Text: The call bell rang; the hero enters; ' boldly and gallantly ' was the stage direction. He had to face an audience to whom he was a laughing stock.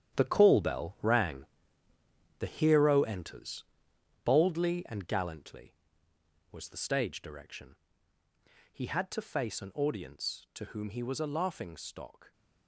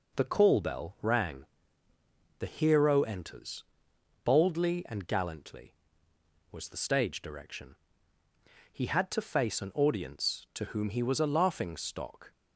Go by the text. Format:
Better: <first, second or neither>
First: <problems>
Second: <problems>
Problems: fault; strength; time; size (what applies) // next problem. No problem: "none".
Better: second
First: gets quieter; strong; throughout; 8 dB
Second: none